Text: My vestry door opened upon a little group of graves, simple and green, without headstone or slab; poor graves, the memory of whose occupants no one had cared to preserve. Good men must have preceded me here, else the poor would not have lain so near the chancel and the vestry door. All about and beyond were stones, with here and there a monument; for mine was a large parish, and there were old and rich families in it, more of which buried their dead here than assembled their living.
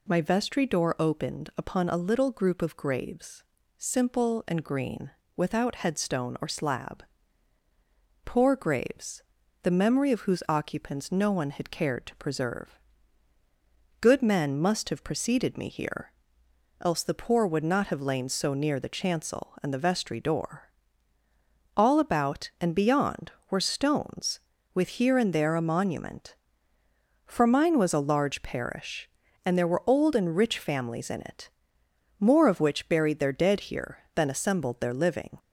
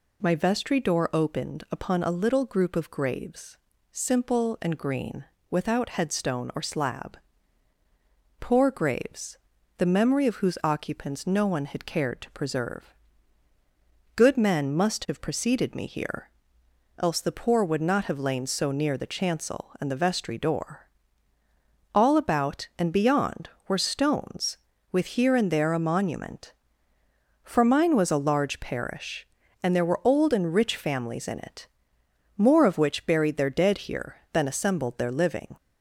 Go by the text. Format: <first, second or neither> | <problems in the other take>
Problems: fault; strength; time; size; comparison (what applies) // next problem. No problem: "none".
neither | none